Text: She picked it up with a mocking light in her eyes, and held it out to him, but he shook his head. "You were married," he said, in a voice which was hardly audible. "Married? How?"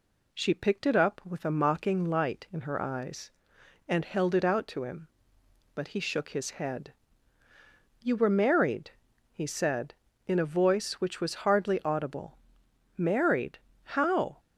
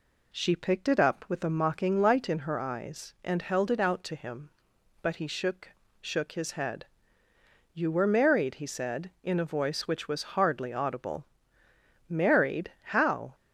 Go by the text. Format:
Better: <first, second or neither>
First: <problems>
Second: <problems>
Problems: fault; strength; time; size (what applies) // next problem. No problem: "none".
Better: first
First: none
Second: says "shook" twice; at 6.0 s